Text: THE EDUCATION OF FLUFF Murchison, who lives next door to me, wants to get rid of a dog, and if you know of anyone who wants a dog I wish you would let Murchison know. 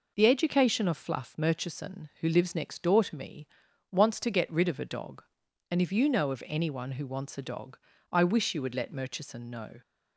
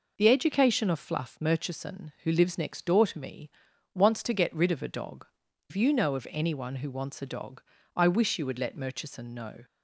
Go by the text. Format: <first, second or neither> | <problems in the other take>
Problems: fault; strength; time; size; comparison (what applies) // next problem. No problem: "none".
first | skips "and"; at 5.4 s // pauses between "dog" and "I"; slight; at 7.6 s; 0.34 s long; slight in the first